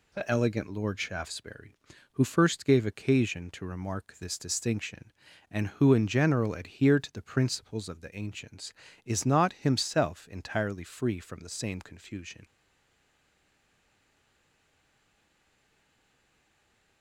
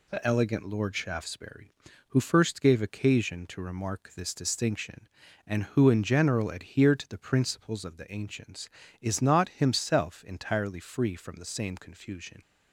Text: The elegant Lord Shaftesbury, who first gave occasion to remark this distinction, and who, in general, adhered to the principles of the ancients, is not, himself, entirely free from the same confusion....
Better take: second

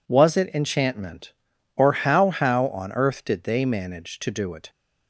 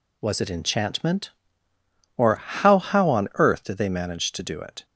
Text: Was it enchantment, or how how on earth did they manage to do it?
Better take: neither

